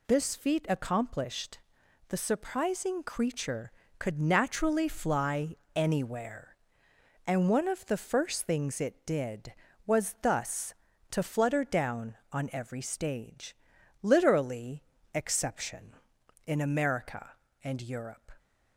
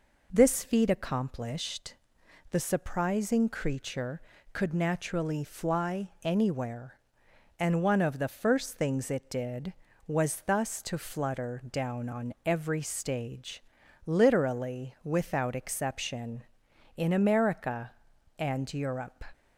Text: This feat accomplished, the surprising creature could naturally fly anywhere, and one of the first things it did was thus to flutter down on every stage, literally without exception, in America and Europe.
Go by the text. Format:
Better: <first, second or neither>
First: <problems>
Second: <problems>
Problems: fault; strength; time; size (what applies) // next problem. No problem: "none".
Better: second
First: pauses between "fly" and "anywhere"; slight; at 5.5 s; 0.20 s long // skips "without"; at 14.9 s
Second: none